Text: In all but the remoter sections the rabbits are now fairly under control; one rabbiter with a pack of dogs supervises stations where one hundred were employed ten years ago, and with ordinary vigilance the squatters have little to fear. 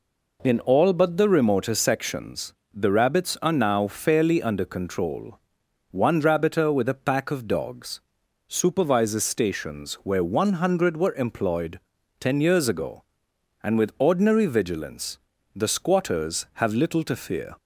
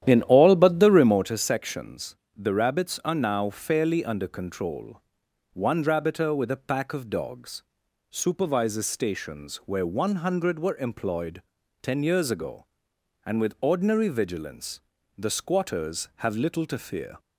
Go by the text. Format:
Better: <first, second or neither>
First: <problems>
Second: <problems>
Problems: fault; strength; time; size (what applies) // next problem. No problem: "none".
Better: first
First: pauses between "sections" and "the"; slight; at 2.5 s; 0.20 s long // pauses between "dogs" and "supervises"; noticeable; at 8.0 s; 0.46 s long // pauses between "employed" and "ten"; at 11.7 s; 0.40 s long // pauses between "vigilance" and "the"; slight; at 15.1 s; 0.36 s long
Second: starts louder than the rest; strong; until 1.3 s; 10.5 dB // pauses between "sections" and "the"; slight; at 2.1 s; 0.20 s long // pauses between "dogs" and "supervises"; noticeable; at 7.6 s; 0.46 s long // pauses between "employed" and "ten"; at 11.4 s; 0.40 s long // pauses between "vigilance" and "the"; slight; at 14.8 s; 0.36 s long